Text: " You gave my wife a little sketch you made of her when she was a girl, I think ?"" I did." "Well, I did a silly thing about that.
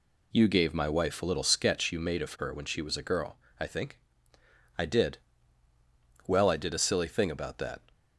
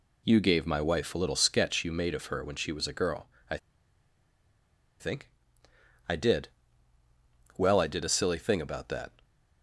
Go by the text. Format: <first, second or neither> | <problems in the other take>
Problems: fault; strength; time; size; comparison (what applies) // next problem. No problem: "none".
first | pauses between "I" and "think"; strong; at 3.5 s; 1.4 s long